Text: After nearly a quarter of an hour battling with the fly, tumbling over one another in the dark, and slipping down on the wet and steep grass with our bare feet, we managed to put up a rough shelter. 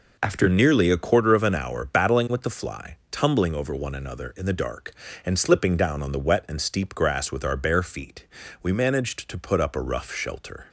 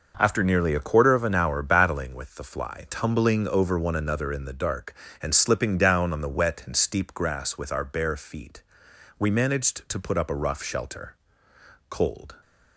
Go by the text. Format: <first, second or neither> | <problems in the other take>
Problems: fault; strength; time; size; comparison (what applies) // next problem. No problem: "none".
first | goes on to say "Cold"; slight; from 11.8 s on; 0.48 s long